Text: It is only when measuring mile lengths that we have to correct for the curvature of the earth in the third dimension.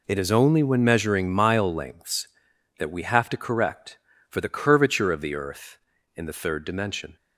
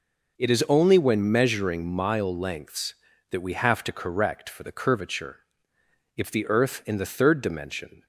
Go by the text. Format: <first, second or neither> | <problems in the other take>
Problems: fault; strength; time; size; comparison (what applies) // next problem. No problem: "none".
first | says "if" for "of"; at 6.1 s